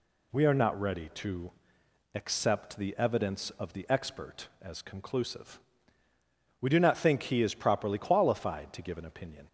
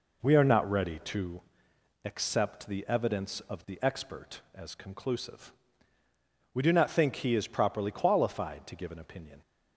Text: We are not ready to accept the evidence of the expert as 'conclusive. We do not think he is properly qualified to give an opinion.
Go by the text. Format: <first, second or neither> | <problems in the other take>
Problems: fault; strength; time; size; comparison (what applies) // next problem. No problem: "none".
first | starts louder than the rest; noticeable; until 1.3 s; 4 dB // pauses between "to" and "accept"; noticeable; at 1.4 s; 0.62 s long; noticeable in the first